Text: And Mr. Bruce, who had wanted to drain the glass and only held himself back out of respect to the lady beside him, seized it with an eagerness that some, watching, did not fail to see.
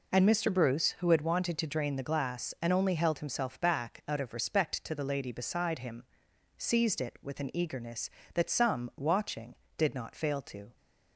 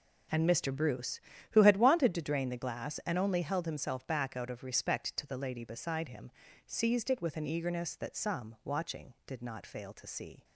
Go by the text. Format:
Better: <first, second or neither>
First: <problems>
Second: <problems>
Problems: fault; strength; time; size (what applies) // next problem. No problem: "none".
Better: second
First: stops before "see"; at 10.7 s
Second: none